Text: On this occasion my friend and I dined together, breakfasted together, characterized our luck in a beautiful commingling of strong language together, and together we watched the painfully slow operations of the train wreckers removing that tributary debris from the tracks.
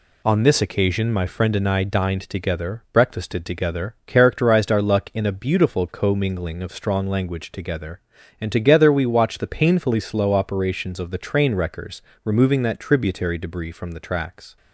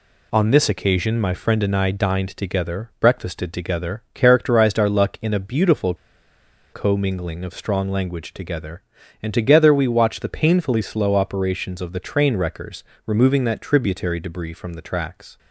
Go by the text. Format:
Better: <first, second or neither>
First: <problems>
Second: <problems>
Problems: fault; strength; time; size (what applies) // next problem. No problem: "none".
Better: first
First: pauses between "wreckers" and "removing"; slight; at 12.0 s; 0.20 s long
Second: pauses between "beautiful" and "commingling"; noticeable; at 5.9 s; 0.78 s long // pauses between "wreckers" and "removing"; slight; at 12.8 s; 0.20 s long